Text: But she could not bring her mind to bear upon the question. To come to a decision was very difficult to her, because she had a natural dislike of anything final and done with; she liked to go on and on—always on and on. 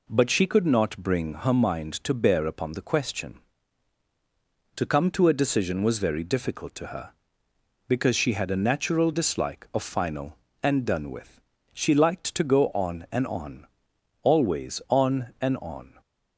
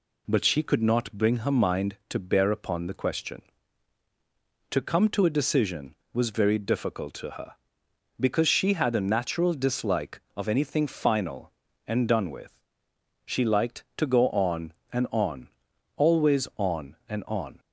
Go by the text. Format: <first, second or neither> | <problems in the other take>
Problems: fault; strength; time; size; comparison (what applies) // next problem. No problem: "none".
second | skips "anything"; at 9.8 s